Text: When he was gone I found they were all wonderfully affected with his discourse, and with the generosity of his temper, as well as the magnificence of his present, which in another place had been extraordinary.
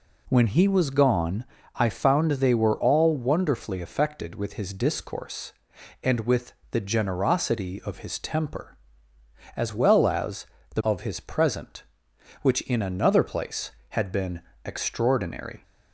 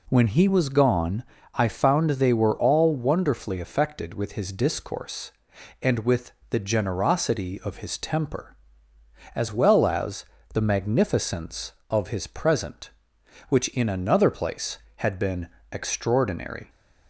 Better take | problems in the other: second | pauses between "gone" and "I"; slight; at 1.4 s; 0.32 s long; slight in the second // pauses between "with" and "the"; slight; at 6.5 s; 0.20 s long; slight in the second // pauses between "as" and "the"; slight; at 10.4 s; 0.28 s long; slight in the second // skips "magnificence"; at 10.8 s // pauses between "been" and "extraordinary"; slight; at 14.4 s; 0.24 s long; slight in the second

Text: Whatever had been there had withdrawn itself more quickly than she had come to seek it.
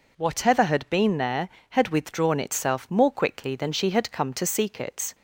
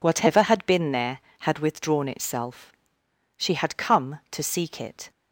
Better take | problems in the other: first | skips "more quickly than"; at 3.0 s

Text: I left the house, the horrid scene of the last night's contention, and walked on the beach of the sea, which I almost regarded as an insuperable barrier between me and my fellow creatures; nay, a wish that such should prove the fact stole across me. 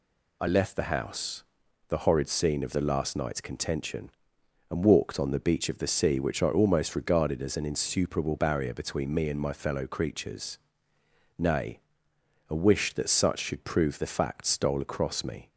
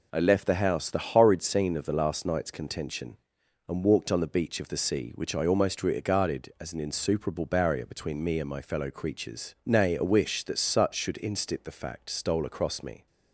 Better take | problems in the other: first | says "instit" for "prove"; at 11.2 s

